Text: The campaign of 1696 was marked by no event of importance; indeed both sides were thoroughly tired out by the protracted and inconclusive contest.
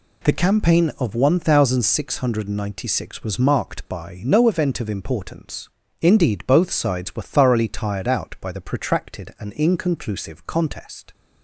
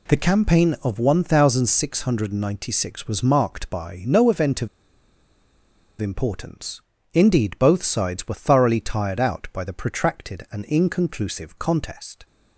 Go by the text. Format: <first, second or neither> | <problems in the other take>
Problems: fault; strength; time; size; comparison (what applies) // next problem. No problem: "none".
first | pauses between "of" and "importance"; strong; at 4.6 s; 1.3 s long